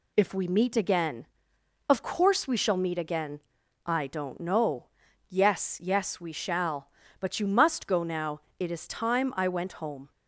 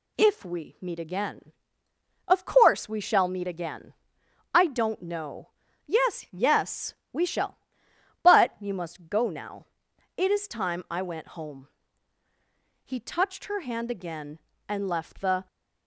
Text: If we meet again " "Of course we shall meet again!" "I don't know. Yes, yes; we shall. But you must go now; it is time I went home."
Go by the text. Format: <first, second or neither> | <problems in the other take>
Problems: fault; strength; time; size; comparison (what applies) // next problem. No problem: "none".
first | goes on to say "He touched her hand again and left the"; strong; from 12.8 s on; 2.6 s long